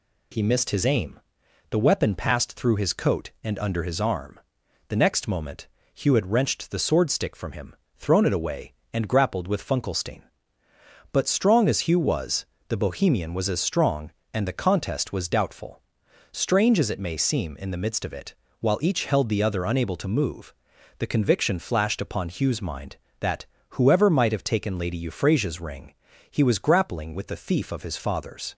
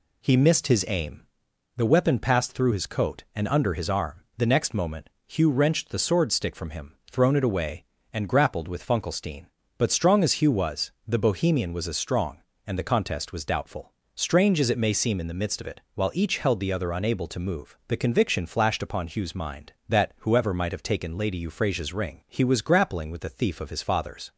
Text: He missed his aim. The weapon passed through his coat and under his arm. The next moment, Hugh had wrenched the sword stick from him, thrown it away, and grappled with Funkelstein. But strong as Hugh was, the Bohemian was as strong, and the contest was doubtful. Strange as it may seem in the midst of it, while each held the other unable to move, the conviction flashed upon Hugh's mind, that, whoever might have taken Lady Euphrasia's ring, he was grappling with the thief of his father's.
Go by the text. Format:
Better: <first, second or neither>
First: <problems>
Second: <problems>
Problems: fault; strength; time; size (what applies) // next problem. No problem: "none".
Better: first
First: none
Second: skips "had"; at 5.4 s